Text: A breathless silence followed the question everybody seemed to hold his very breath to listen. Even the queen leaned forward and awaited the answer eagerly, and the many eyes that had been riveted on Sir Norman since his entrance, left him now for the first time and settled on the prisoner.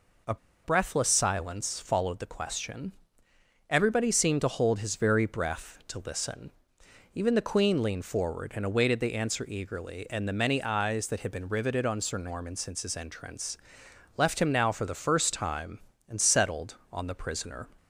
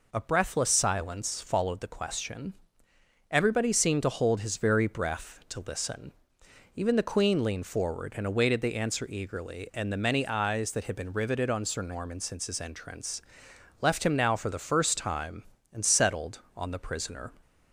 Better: second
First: pauses between "A" and "breathless"; slight; at 0.3 s; 0.29 s long // pauses between "question" and "everybody"; noticeable; at 2.9 s; 0.76 s long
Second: pauses between "question" and "everybody"; noticeable; at 2.5 s; 0.76 s long

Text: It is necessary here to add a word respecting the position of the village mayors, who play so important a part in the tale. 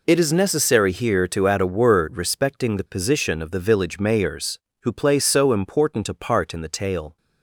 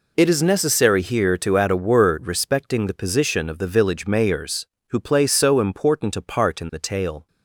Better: neither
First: none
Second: none

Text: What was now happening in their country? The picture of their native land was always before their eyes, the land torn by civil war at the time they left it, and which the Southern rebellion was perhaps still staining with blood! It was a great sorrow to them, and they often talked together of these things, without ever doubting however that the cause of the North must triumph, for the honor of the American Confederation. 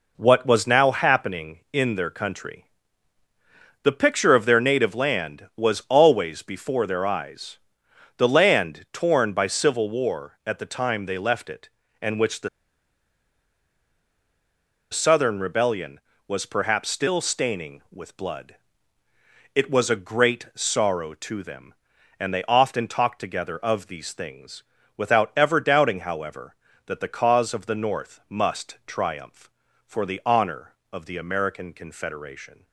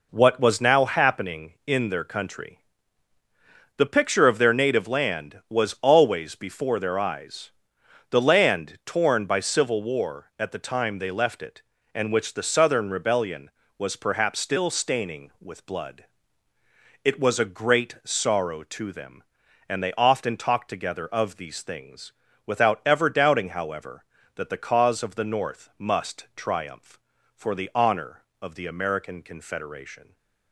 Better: second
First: pauses between "the" and "Southern"; strong; at 12.4 s; 2.4 s long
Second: none

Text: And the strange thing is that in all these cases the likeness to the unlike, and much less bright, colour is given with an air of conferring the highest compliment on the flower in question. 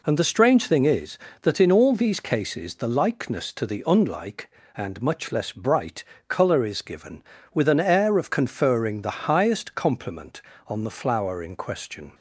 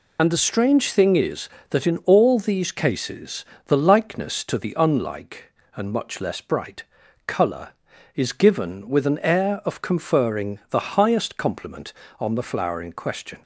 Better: first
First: none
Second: loses the start of "And"; at 0.1 s; 45 ms // pauses between "cases" and "the"; slight; at 3.4 s; 0.20 s long

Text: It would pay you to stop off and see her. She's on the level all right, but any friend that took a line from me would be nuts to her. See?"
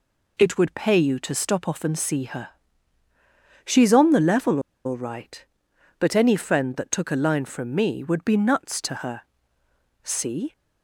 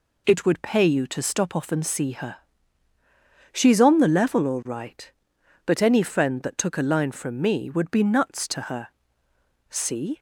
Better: second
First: pauses between "level" and "all"; slight; at 4.5 s; 0.26 s long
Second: none

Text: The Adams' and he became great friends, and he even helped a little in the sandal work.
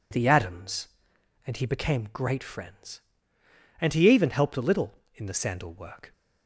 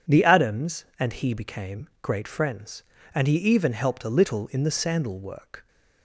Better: neither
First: none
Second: none

